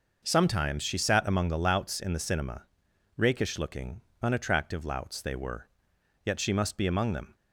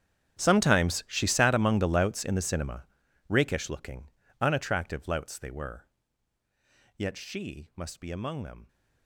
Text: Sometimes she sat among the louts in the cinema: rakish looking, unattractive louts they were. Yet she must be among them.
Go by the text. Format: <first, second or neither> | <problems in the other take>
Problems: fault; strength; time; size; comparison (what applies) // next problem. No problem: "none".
first | gets quieter; strong; throughout; 21 dB